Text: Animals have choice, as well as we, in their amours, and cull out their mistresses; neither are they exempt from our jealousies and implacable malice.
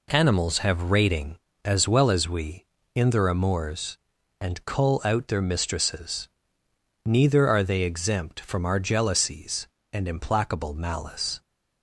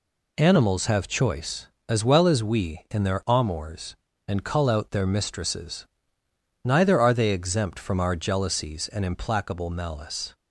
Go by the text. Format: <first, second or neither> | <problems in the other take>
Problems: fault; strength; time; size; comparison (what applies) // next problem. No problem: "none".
second | says "rating" for "choice"; at 0.8 s